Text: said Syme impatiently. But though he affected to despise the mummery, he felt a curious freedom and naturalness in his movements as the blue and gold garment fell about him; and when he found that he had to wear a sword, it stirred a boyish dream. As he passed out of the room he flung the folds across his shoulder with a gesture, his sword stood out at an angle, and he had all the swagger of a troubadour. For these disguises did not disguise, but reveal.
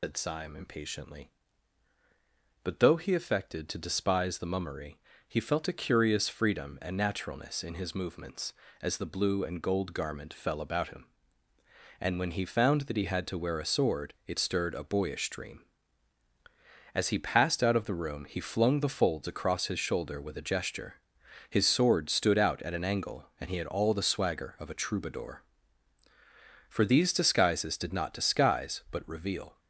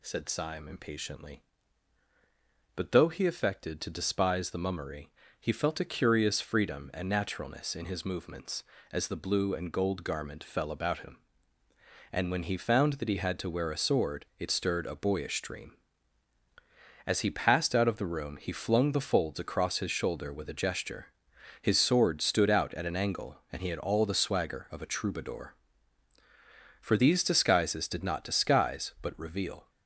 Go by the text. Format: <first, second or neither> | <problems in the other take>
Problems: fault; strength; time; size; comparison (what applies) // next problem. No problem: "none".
second | loses the start of "said"; at 0.0 s; 125 ms